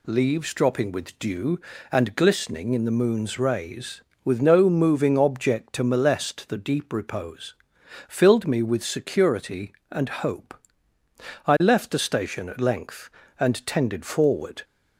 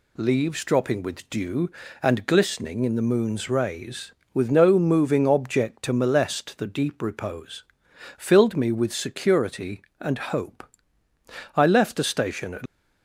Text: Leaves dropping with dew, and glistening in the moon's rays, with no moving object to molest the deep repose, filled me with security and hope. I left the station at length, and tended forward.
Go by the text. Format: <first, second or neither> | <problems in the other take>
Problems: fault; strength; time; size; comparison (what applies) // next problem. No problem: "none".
first | stops before "length and tended forward"; at 12.6 s